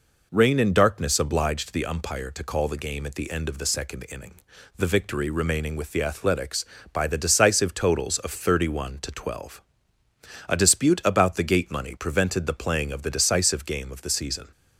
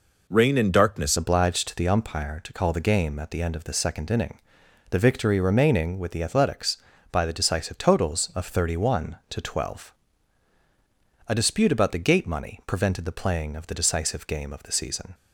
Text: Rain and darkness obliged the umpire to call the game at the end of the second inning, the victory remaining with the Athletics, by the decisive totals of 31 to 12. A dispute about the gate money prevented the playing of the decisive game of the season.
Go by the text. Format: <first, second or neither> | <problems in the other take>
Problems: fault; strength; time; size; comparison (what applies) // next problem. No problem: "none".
first | changes voice at "obliged"; from 1.1 s on; 14.0 s long